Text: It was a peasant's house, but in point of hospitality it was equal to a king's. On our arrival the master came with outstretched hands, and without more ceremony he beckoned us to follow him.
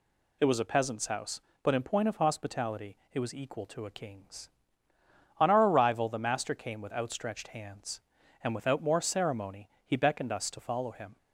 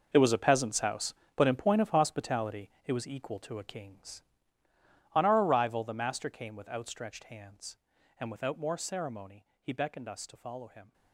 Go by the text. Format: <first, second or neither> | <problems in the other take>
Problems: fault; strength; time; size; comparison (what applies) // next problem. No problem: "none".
first | gets quieter; strong; throughout; 14 dB // pauses between "hospitality" and "it"; slight; at 2.6 s; 0.16 s long; slight in the first // pauses between "ceremony" and "he"; slight; at 9.4 s; 0.16 s long; slight in the first